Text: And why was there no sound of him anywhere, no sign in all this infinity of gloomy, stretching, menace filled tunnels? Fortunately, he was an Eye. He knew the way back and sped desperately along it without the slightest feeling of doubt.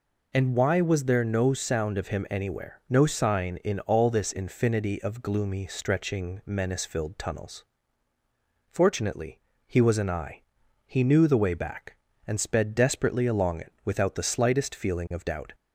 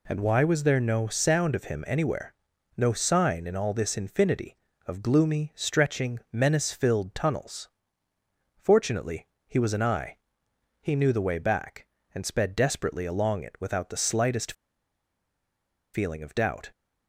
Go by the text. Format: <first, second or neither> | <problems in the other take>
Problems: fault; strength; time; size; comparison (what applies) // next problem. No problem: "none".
first | pauses between "slightest" and "feeling"; strong; at 14.5 s; 1.4 s long